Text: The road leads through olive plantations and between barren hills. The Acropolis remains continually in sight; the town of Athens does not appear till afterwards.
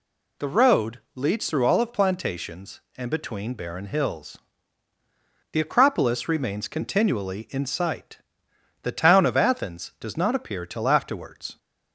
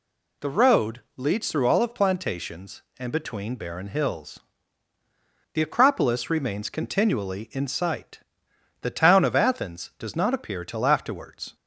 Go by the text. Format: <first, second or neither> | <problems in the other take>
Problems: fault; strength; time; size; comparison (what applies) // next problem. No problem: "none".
neither | pauses between "road" and "leads"; slight; the same in both